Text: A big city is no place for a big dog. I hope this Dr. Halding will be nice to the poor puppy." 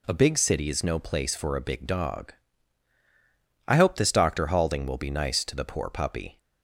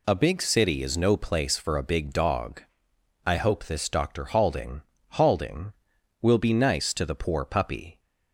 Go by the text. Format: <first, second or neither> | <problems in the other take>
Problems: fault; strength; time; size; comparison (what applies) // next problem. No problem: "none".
first | says "Halding" twice; at 5.1 s